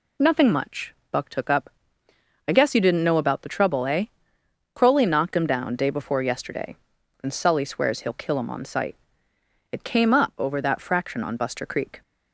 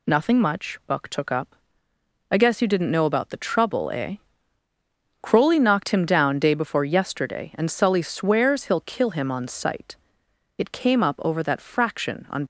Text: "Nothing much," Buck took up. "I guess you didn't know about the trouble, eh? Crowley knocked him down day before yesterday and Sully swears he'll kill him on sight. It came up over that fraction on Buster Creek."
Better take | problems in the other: first | stops before "Buster Creek"; at 12.4 s

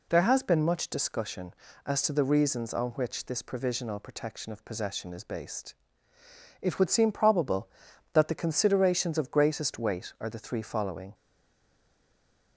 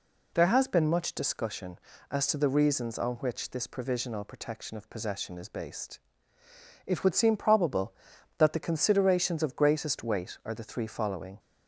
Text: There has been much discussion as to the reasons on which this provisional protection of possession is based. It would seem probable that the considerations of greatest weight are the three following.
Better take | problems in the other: second | stays silent after the last word; noticeable; from 11.1 s on; 1.4 s long

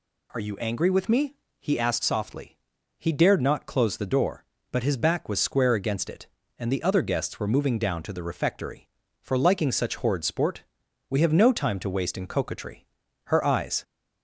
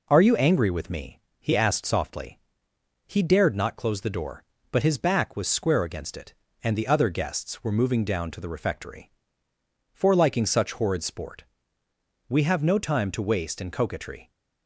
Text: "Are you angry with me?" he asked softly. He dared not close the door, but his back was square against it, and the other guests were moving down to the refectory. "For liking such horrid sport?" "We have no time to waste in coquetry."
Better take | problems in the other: second | goes on to say "Her eyes"; from 13.2 s on; 0.58 s long

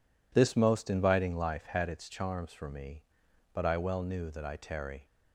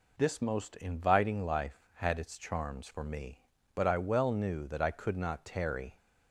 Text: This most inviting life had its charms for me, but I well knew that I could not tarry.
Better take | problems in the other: second | skips "could not"; at 4.5 s

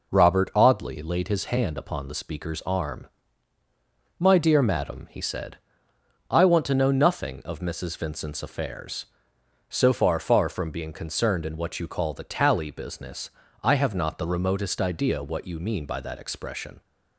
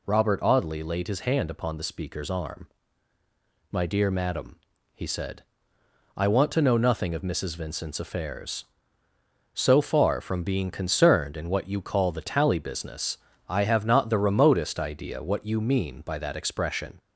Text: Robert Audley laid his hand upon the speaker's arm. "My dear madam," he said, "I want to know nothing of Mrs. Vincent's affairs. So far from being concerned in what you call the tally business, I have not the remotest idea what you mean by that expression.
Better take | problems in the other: second | says "far" twice; at 10.1 s

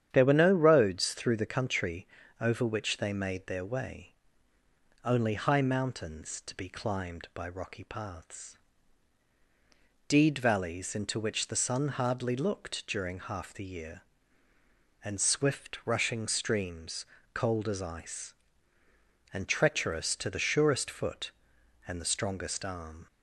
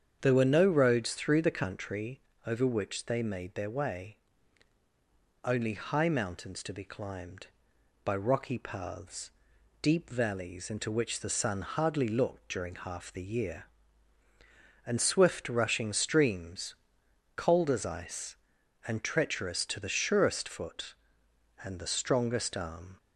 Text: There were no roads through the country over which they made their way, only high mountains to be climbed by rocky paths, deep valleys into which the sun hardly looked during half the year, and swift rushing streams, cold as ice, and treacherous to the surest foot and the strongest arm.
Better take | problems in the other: second | starts louder than the rest; strong; until 1.1 s; 9.5 dB; strong in the second // pauses between "country" and "over"; slight; at 2.0 s; 0.36 s long; slight in the second // says "deed" for "deep"; at 10.0 s

